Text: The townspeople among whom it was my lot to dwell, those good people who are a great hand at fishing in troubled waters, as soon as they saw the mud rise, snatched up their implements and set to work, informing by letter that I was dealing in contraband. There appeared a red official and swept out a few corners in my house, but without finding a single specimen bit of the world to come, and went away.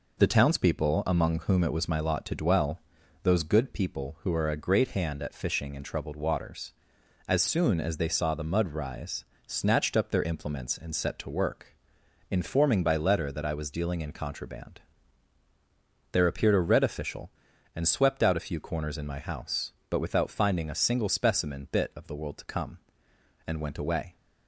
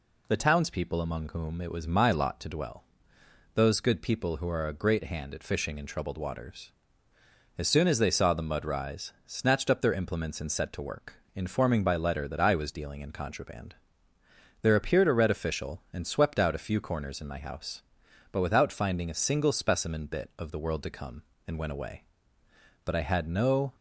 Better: first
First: none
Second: goes on to say "But I had no"; noticeable; from 22.8 s on; 0.88 s long

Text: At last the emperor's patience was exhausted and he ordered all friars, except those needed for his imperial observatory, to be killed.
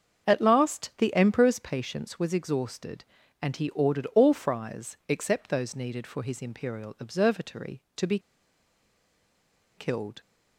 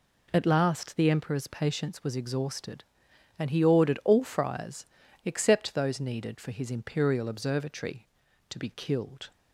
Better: second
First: starts louder than the rest; until 1.3 s; 6.5 dB // pauses between "be" and "killed"; strong; at 8.1 s; 1.5 s long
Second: none

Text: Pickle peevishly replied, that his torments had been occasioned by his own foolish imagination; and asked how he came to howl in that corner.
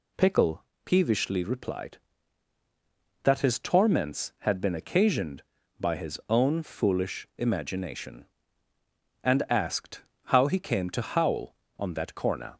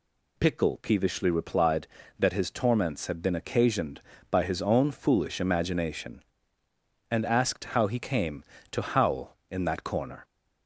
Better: second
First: pauses between "Pickle" and "peevishly"; slight; at 0.6 s; 0.20 s long // pauses between "asked" and "how"; slight; at 10.0 s; 0.24 s long // says "on" for "in"; at 11.7 s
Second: none

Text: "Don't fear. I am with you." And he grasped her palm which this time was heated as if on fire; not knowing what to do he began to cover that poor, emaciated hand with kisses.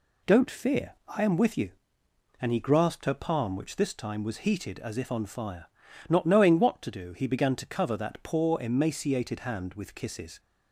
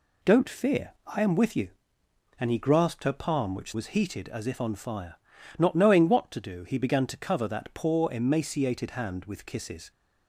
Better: first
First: none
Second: skips "this time"; at 3.7 s

